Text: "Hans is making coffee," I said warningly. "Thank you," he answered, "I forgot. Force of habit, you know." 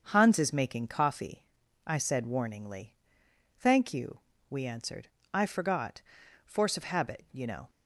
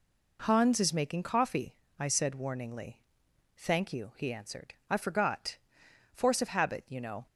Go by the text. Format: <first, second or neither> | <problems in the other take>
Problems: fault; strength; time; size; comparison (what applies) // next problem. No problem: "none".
second | starts louder than the rest; until 1.0 s; 6.5 dB // says "we" for "he"; at 4.4 s